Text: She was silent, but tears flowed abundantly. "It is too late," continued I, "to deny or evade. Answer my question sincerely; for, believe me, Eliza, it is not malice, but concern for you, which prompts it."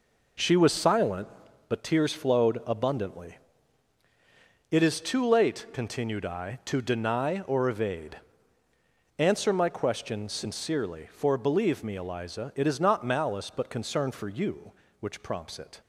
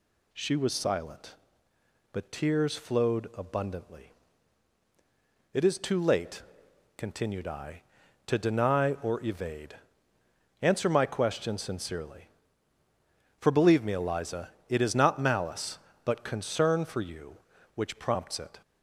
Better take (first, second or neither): second